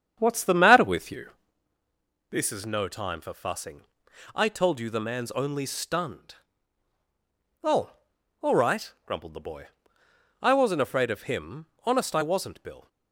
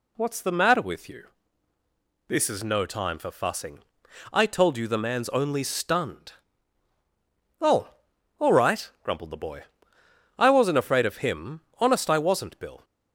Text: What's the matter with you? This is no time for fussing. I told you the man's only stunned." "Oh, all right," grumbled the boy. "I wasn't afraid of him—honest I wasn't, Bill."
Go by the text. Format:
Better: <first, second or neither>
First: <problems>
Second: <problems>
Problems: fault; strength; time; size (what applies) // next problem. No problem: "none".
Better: second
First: starts louder than the rest; strong; until 1.7 s; 8 dB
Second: none